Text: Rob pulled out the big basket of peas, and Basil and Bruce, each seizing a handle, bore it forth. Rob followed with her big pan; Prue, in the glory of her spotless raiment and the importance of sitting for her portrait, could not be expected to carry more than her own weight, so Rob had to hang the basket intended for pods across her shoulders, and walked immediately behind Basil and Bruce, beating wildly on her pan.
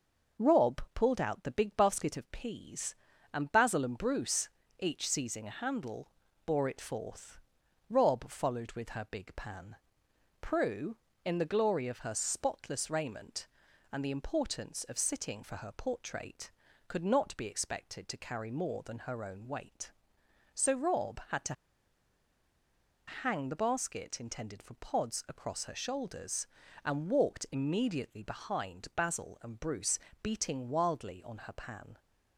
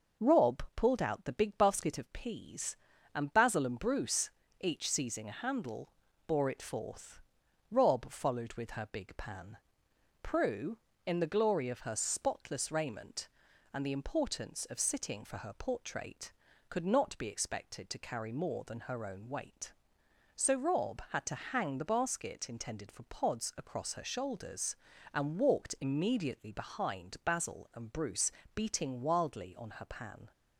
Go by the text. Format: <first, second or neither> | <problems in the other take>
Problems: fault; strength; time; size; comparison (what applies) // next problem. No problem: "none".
second | pauses between "to" and "hang"; strong; at 21.5 s; 1.5 s long